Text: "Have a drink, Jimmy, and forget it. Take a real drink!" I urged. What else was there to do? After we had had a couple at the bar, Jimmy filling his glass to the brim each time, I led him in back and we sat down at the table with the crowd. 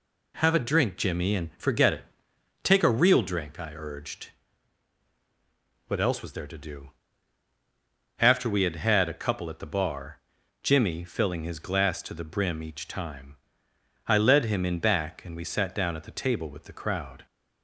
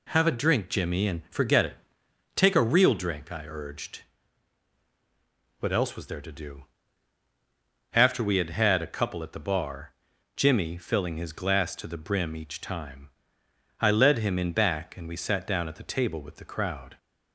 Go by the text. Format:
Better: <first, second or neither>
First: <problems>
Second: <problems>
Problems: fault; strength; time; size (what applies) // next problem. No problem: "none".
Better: neither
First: none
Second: none